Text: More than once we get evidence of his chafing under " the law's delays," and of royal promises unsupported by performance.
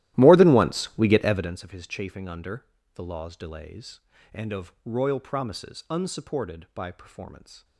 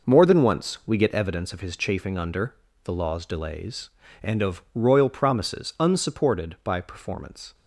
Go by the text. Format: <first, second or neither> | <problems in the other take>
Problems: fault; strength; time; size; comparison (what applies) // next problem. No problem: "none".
second | starts louder than the rest; strong; until 1.6 s; 15 dB